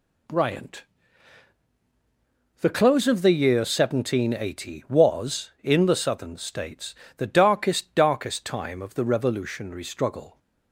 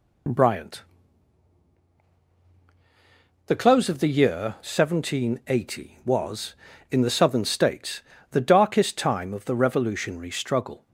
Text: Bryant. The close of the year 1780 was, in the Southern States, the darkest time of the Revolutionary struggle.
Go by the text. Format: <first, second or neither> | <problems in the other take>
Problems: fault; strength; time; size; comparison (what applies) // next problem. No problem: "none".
second | says "darkest" twice; at 7.9 s